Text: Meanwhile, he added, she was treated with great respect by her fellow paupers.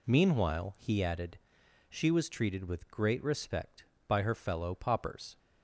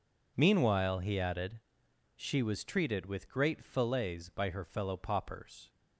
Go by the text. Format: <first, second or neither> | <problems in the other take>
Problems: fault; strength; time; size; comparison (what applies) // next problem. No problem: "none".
first | says "fillets" for "respect"; at 3.6 s